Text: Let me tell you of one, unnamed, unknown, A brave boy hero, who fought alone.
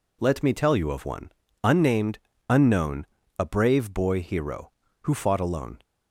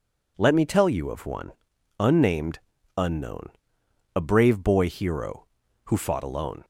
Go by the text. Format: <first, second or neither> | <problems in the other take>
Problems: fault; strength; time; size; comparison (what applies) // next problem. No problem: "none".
neither | none